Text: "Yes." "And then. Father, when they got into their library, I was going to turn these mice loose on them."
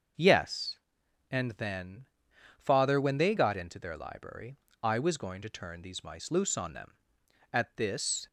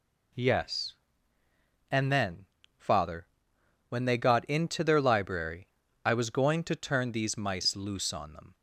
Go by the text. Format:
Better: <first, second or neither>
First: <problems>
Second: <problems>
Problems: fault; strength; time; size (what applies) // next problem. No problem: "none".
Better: second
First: starts louder than the rest; until 1.7 s; 6.5 dB // goes on to say "At this"; noticeable; from 7.5 s on; 0.74 s long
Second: none